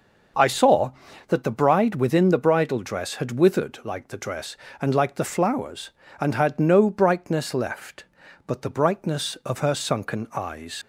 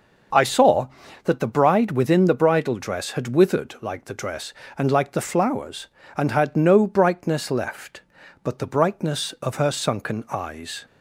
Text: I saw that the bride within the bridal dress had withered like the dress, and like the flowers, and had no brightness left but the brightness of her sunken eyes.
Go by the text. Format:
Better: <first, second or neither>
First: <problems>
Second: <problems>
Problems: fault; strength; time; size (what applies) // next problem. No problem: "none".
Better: second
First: starts louder than the rest; noticeable; until 1.7 s; 6 dB // leaves "eyes" unfinished; at 10.8 s; 70 ms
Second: starts louder than the rest; noticeable; until 1.7 s; 6 dB